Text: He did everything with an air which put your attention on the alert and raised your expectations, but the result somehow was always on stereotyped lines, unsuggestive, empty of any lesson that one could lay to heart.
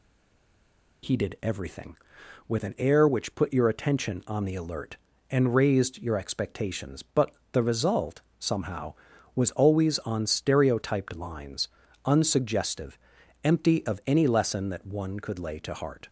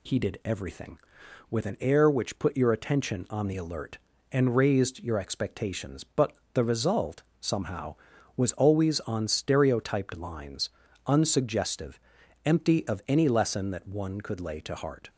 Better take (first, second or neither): second